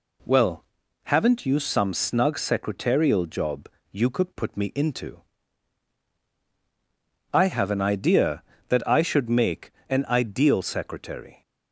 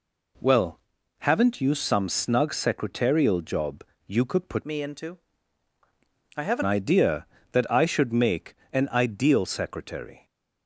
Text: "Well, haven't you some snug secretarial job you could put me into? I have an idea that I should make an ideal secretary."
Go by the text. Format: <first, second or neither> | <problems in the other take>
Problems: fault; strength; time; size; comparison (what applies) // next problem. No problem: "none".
first | pauses between "job" and "you"; slight; at 3.8 s; 0.22 s long; slight in the first // changes voice from "me" to "an"; from 4.6 to 6.6 s; 2.0 s long // pauses between "make" and "an"; slight; at 8.5 s; 0.18 s long; slight in the first